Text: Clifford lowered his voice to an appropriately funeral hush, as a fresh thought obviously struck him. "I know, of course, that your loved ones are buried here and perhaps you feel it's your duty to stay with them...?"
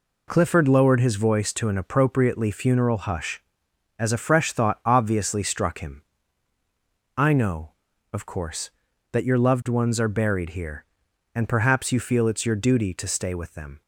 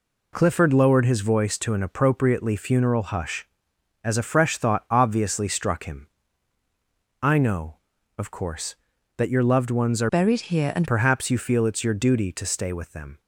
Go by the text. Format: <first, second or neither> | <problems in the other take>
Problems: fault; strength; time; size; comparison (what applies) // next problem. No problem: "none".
first | changes voice from "buried" to "and"; from 10.1 to 10.8 s; 0.7 s long